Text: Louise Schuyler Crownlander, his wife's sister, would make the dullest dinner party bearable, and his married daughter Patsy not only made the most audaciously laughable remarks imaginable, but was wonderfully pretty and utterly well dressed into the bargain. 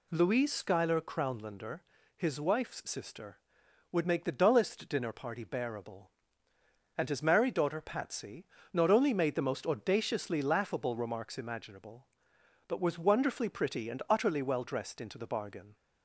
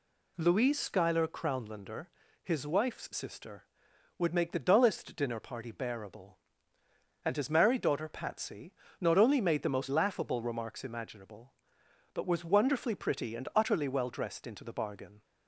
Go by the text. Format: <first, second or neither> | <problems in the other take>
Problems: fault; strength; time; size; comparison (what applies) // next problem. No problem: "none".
first | pauses between "Patsy" and "not"; slight; at 8.7 s; 0.26 s long; slight in the first // skips "audaciously"; at 9.8 s